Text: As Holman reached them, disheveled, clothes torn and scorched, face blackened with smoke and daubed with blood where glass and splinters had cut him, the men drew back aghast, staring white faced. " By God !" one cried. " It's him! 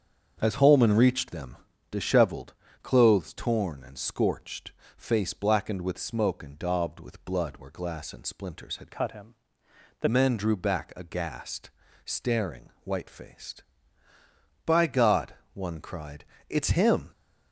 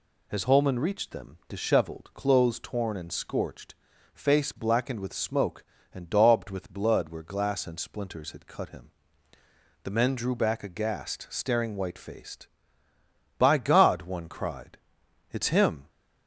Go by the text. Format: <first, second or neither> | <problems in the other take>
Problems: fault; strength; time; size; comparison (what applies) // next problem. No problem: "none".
second | starts louder than the rest; strong; until 1.4 s; 7.5 dB // changes voice from "cut" to "the"; from 8.9 to 10.0 s; 1.1 s long